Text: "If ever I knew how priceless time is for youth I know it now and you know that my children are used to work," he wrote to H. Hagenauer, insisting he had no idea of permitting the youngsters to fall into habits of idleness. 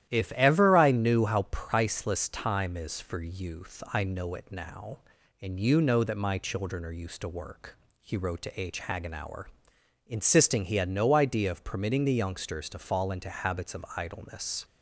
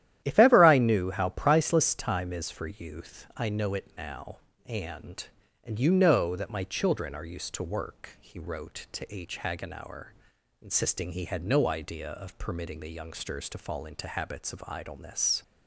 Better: first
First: starts louder than the rest; strong; until 1.1 s; 12 dB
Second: starts louder than the rest; strong; until 1.2 s; 12 dB // says "and" twice; at 5.6 s

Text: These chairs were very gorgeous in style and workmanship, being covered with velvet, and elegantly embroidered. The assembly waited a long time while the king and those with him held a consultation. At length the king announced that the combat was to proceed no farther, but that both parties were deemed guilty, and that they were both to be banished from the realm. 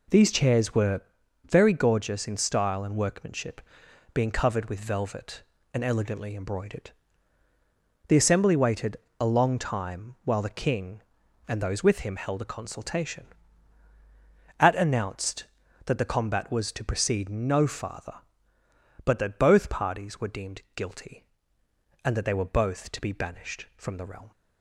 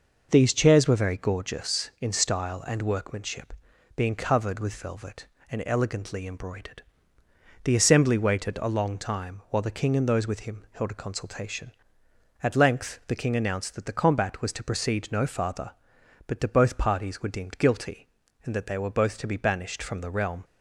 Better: second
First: pauses between "were" and "very"; at 1.0 s; 0.44 s long // pauses between "waited" and "a"; slight; at 8.9 s; 0.24 s long // skips "length the king"; at 14.7 s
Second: none

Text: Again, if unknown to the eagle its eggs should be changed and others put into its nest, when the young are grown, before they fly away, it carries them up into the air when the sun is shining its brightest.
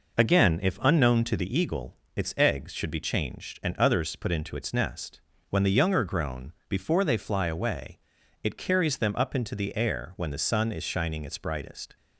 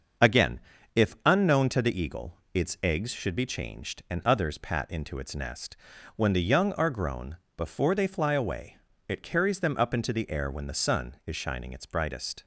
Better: first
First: pauses between "eagle" and "its"; slight; at 1.9 s; 0.18 s long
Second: starts louder than the rest; until 1.6 s; 6.5 dB // pauses between "eagle" and "its"; slight; at 2.3 s; 0.18 s long // says "pat" for "put"; at 4.5 s

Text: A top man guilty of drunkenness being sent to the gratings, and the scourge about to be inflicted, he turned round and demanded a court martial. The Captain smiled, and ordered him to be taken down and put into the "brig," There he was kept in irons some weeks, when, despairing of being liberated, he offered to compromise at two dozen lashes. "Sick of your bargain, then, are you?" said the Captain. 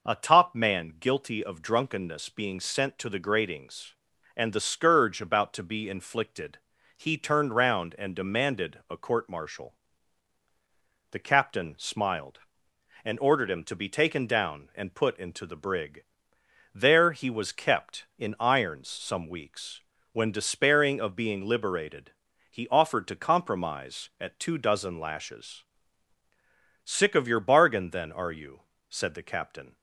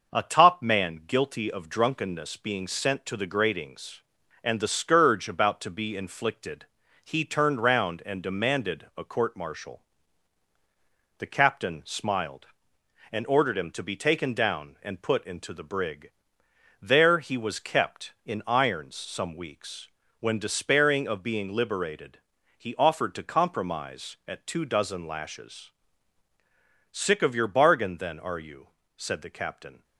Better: first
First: none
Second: gets quieter; slight; throughout; 3.5 dB

